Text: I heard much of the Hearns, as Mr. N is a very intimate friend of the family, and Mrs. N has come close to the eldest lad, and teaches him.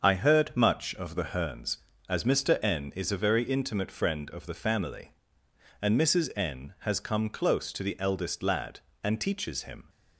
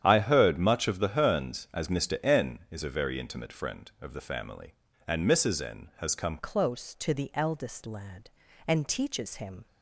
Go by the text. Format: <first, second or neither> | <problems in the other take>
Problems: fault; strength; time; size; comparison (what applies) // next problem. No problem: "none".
first | starts louder than the rest; strong; until 1.0 s; 9.5 dB; also in the first // changes voice at "close"; from 6.3 s on; 3.3 s long